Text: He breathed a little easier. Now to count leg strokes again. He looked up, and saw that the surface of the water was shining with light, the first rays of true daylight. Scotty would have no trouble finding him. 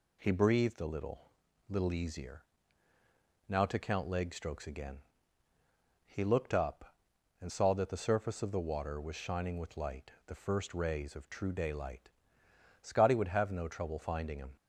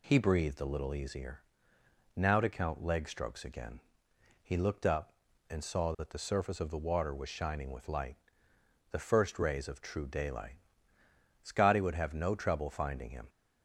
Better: second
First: says "little" twice; at 1.6 s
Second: none

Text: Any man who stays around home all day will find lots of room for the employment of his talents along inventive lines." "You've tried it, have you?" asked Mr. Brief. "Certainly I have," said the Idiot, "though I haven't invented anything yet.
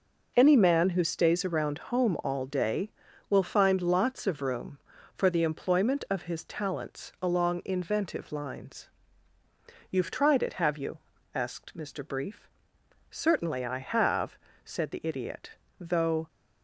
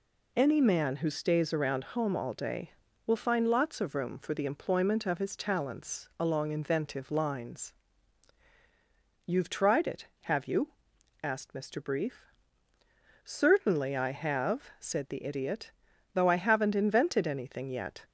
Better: second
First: stops before "I haven't invented anything yet"; at 16.2 s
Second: none

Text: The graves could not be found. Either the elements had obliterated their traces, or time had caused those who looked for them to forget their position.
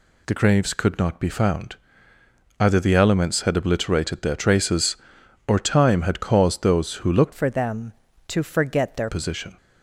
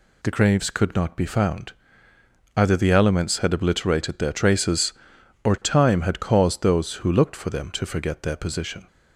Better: second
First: changes voice from "for" to "their"; from 7.3 to 9.0 s; 1.7 s long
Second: none

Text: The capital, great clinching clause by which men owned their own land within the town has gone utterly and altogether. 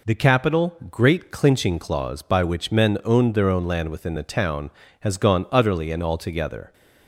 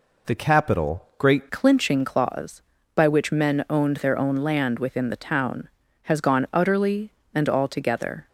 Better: first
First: none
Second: changes voice at "clinching"; from 1.4 s on; 6.8 s long

